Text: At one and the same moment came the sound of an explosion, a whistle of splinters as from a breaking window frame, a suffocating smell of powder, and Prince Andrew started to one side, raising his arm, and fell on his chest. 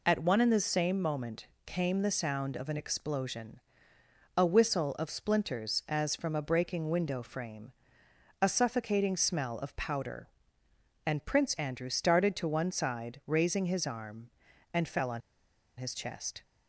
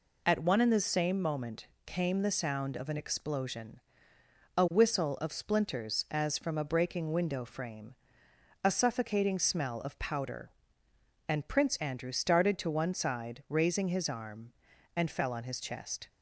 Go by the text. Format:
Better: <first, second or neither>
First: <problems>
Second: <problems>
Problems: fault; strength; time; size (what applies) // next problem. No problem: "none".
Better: second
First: pauses between "moment" and "came"; slight; at 1.4 s; 0.18 s long // pauses between "on" and "his"; noticeable; at 15.2 s; 0.57 s long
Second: pauses between "moment" and "came"; slight; at 1.6 s; 0.18 s long